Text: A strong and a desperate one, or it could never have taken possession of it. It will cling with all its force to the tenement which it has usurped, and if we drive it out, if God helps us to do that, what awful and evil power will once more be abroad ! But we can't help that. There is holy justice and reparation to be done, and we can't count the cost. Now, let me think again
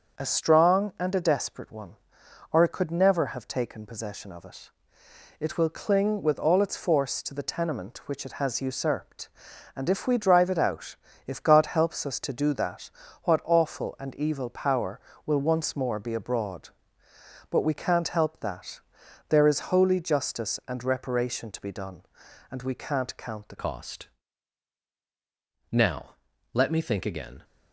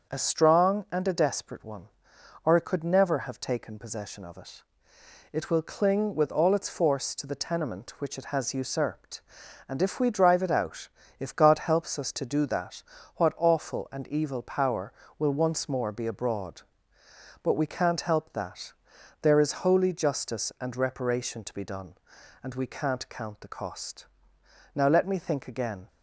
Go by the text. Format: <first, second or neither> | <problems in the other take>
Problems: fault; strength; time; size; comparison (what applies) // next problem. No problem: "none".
second | starts louder than the rest; until 1.2 s; 6.5 dB; also in the second // changes voice at "cost"; from 23.5 s on; 3.9 s long